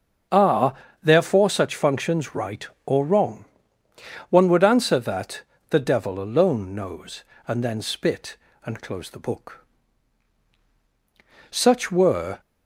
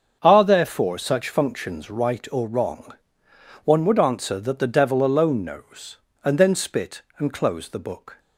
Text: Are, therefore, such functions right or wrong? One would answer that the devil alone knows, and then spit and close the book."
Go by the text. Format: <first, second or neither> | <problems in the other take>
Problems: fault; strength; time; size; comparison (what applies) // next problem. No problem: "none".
second | starts louder than the rest; until 1.5 s; 6.5 dB; also in the second // pauses between "that" and "the"; slight; at 5.4 s; 0.28 s long // goes on to say "Such were"; noticeable; from 11.4 s on; 0.90 s long